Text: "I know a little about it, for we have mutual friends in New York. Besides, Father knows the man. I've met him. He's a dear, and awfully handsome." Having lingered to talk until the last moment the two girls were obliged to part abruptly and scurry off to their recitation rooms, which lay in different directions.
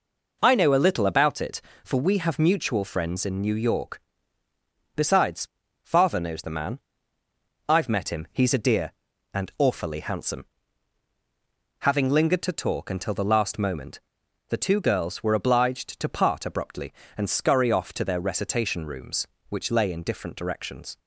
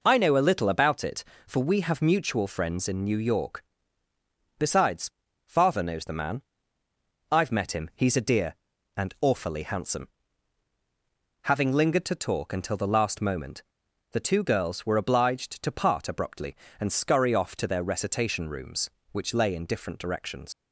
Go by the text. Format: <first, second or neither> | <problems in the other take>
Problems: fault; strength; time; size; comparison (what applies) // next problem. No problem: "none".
first | pauses between "moment" and "the"; noticeable; at 13.6 s; 0.48 s long; noticeable in the first // leaves "directions" unfinished; at 20.5 s; 90 ms